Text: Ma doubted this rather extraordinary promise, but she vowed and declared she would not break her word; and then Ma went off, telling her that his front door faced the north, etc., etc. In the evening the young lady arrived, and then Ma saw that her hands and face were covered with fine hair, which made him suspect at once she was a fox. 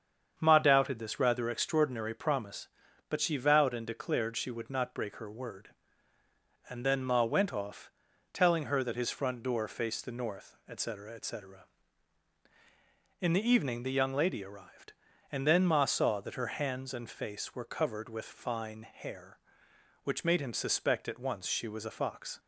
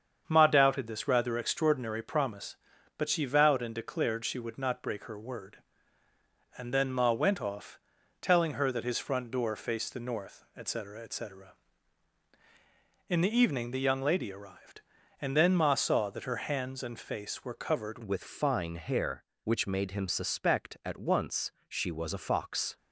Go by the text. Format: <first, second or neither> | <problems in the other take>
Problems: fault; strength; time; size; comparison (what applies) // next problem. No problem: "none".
first | starts louder than the rest; strong; until 1.2 s; 7.5 dB; strong in the first // changes voice at "with"; from 18.0 s on; 4.7 s long // pauses between "once" and "she"; slight; at 21.5 s; 0.16 s long